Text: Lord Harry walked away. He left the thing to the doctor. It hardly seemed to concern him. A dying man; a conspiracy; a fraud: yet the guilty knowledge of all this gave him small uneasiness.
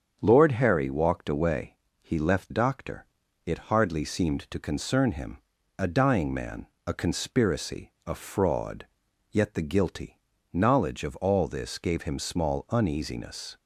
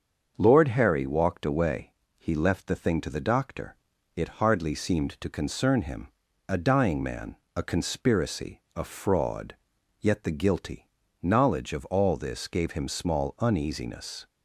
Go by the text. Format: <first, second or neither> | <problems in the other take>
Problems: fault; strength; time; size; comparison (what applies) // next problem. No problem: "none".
second | starts louder than the rest; strong; until 1.2 s; 7.5 dB; also in the second // skips "the thing to the"; at 2.5 s // pauses between "guilty" and "knowledge"; slight; at 10.1 s; 0.34 s long; slight in the second